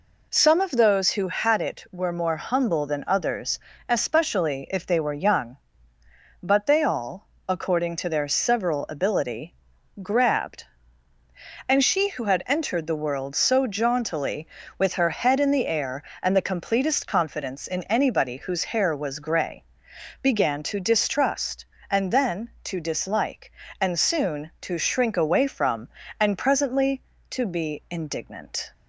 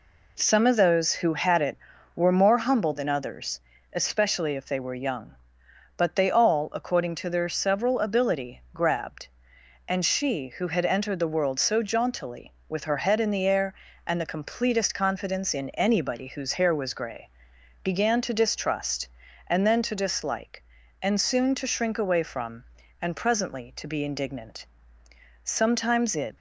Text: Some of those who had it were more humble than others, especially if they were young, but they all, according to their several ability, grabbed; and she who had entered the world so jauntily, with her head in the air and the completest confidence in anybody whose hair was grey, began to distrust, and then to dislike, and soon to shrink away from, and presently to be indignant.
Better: first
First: none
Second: goes on to say "Sometimes it"; noticeable; from 25.4 s on; 0.92 s long

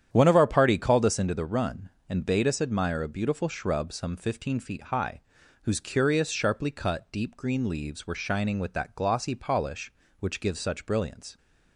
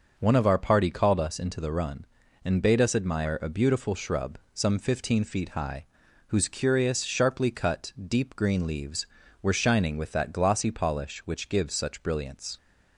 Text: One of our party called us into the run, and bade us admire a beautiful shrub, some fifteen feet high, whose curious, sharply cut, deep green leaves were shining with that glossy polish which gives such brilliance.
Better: second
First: starts louder than the rest; strong; until 1.3 s; 9.5 dB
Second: none

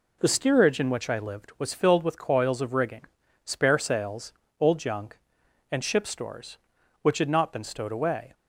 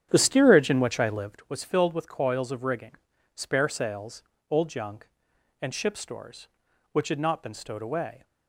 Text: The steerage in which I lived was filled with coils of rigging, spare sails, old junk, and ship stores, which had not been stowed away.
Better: first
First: none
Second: starts louder than the rest; strong; until 1.5 s; 9 dB

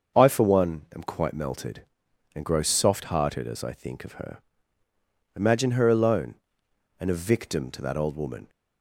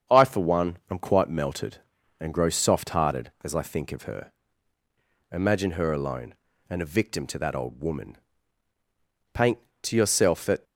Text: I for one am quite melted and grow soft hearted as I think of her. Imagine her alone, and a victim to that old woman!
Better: first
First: starts louder than the rest; until 1.2 s; 6.5 dB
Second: starts louder than the rest; strong; until 1.2 s; 7.5 dB // goes on to say "Paint to yourself that"; noticeable; from 9.3 s on; 1.3 s long

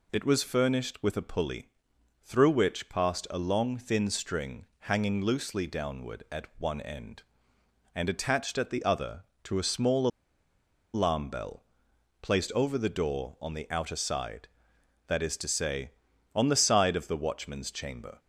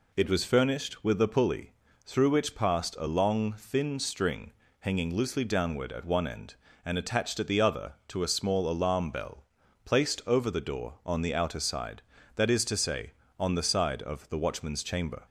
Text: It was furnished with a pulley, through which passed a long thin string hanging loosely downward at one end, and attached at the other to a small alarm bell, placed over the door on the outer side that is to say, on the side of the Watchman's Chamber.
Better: second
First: pauses between "string" and "hanging"; slight; at 4.6 s; 0.18 s long // pauses between "small" and "alarm"; noticeable; at 10.0 s; 0.86 s long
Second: pauses between "string" and "hanging"; slight; at 4.5 s; 0.28 s long

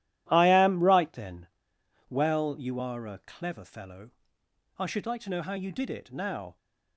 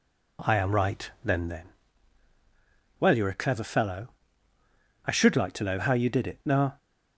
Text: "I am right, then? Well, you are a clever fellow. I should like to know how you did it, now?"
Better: first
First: none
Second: says "then" twice; at 1.4 s

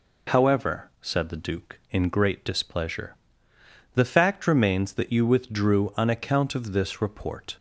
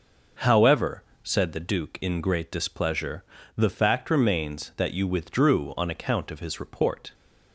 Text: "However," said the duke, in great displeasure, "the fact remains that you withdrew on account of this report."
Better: first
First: none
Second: says "his" for "this"; at 6.4 s

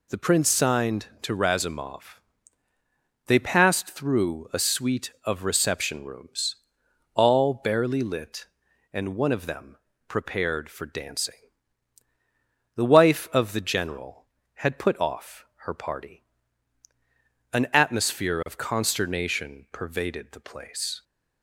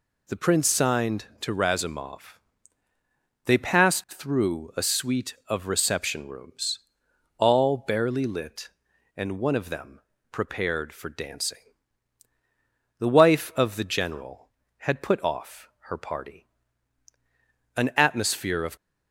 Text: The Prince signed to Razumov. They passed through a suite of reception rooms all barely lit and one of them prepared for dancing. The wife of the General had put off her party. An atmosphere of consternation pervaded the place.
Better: first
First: pauses between "rooms" and "all"; noticeable; at 6.5 s; 0.58 s long // pauses between "them" and "prepared"; slight; at 9.7 s; 0.30 s long // pauses between "off" and "her"; slight; at 15.4 s; 0.22 s long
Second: pauses between "rooms" and "all"; noticeable; at 6.7 s; 0.58 s long // pauses between "them" and "prepared"; slight; at 9.9 s; 0.30 s long // pauses between "off" and "her"; slight; at 15.6 s; 0.22 s long // stops before "consternation pervaded the place"; at 18.7 s

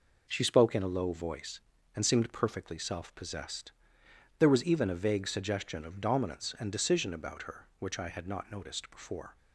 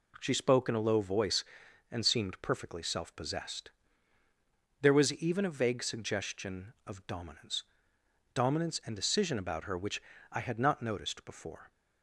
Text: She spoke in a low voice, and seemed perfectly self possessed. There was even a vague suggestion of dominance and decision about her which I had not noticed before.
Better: first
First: none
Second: says "dominance" twice; at 8.3 s // pauses between "which" and "I"; slight; at 10.0 s; 0.30 s long

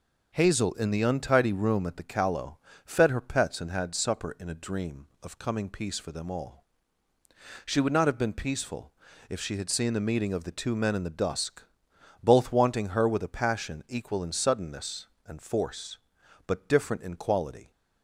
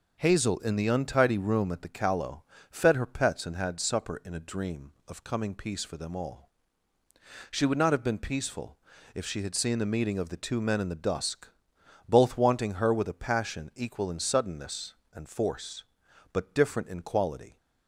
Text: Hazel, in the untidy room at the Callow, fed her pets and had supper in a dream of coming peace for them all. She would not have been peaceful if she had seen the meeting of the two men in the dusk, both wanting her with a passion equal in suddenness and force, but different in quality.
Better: neither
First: pauses between "peaceful" and "if"; slight; at 8.9 s; 0.36 s long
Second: pauses between "peaceful" and "if"; slight; at 8.7 s; 0.36 s long

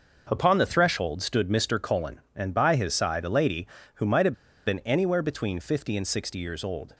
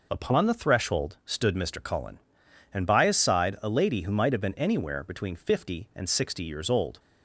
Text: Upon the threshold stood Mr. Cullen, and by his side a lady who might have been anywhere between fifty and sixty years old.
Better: second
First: starts louder than the rest; noticeable; until 1.3 s; 6 dB // pauses between "have" and "been"; slight; at 4.3 s; 0.32 s long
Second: none

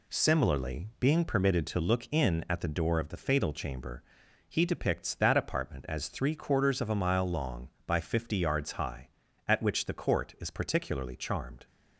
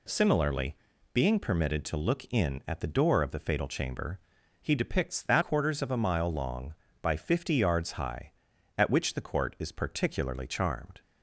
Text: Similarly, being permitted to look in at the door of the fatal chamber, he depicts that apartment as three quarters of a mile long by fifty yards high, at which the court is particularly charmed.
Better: first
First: none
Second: skips "apartment as three"; at 5.4 s

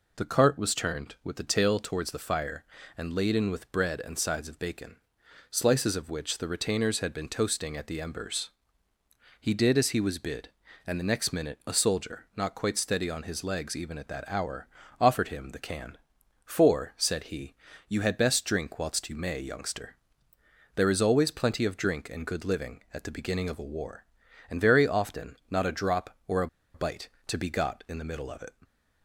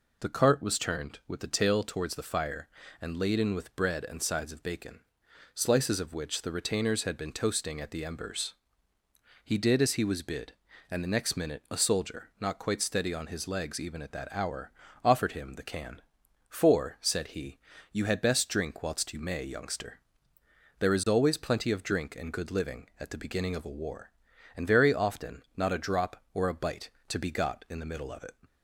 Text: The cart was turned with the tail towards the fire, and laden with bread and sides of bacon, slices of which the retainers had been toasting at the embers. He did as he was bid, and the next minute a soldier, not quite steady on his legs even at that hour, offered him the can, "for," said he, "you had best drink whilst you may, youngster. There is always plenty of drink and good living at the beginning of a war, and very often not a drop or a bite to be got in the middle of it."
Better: second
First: pauses between "a" and "bite"; slight; at 26.4 s; 0.27 s long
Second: none

